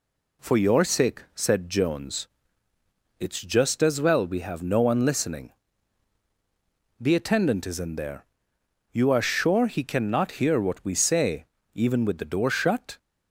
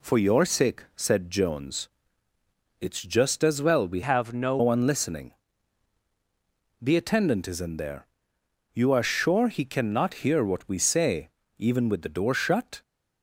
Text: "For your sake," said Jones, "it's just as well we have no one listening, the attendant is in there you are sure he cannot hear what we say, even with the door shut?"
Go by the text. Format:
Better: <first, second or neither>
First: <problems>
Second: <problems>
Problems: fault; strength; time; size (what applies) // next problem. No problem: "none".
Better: first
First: pauses between "there" and "you"; noticeable; at 8.2 s; 0.68 s long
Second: changes voice from "have" to "no"; from 4.0 to 4.5 s; 0.5 s long // pauses between "there" and "you"; noticeable; at 8.0 s; 0.68 s long